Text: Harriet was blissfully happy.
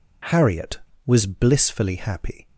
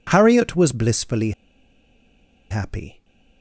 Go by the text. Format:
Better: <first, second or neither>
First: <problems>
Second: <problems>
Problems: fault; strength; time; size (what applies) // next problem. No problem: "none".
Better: first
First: none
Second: pauses between "blissfully" and "happy"; at 1.3 s; 1.1 s long